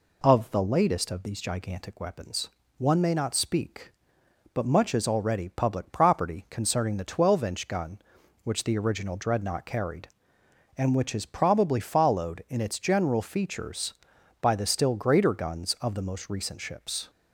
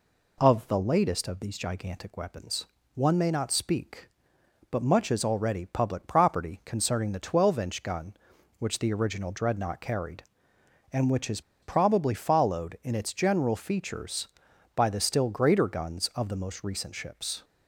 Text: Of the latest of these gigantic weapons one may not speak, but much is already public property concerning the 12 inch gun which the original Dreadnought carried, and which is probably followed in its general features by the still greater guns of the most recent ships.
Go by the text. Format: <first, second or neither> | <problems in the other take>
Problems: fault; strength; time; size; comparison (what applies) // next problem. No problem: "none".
first | pauses between "weapons" and "one"; slight; at 2.6 s; 0.30 s long; slight in the first // pauses between "is" and "probably"; slight; at 11.4 s; 0.20 s long